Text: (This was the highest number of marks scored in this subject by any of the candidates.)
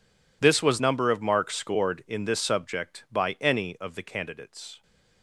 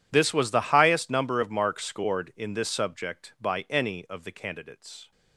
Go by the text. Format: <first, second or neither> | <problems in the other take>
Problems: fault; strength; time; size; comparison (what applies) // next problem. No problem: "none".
second | skips "the highest"; at 0.7 s